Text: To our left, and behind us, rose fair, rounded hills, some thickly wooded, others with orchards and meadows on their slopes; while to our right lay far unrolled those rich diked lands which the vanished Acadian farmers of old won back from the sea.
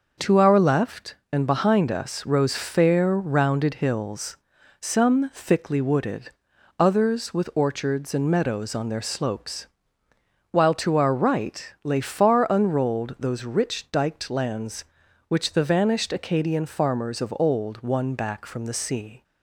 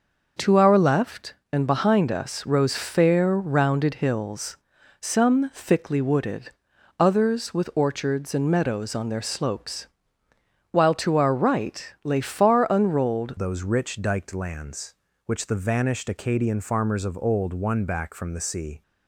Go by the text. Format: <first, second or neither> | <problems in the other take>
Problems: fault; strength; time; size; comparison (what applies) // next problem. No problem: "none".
first | changes voice at "those"; from 13.3 s on; 5.5 s long